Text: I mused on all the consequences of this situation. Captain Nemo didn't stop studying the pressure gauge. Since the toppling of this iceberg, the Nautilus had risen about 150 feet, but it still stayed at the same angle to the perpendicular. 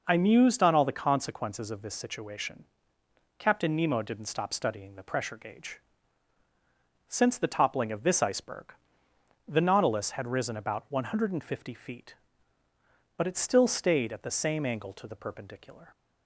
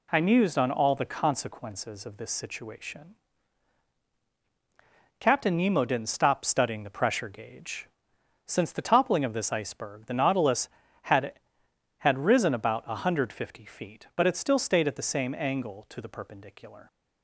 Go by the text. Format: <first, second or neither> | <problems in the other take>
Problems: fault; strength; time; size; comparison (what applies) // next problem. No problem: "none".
first | says "had" twice; at 12.0 s